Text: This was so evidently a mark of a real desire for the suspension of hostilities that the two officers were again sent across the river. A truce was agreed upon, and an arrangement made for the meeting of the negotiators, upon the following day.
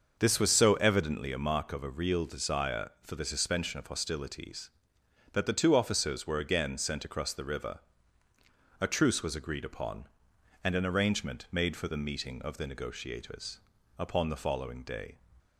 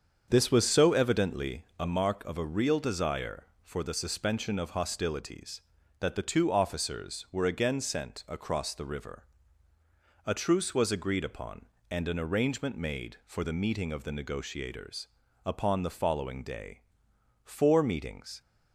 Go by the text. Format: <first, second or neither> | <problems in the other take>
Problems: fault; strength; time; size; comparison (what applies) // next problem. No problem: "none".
first | starts louder than the rest; strong; until 1.2 s; 7 dB; also in the first // goes on to say "Four meetings"; noticeable; from 17.4 s on; 0.96 s long